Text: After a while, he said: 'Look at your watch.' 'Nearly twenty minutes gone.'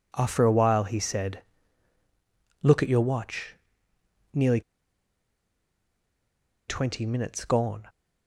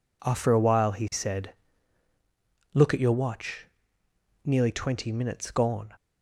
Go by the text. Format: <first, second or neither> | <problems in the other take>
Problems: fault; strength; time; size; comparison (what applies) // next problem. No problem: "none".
second | pauses between "Nearly" and "twenty"; strong; at 4.5 s; 2.0 s long